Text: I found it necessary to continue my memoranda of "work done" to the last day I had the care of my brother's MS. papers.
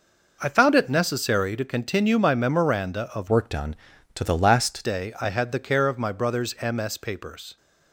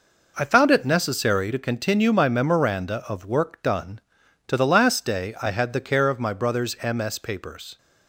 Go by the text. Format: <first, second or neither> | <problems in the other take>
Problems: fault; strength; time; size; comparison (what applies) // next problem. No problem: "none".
second | changes voice from "work" to "last"; from 3.2 to 4.8 s; 1.6 s long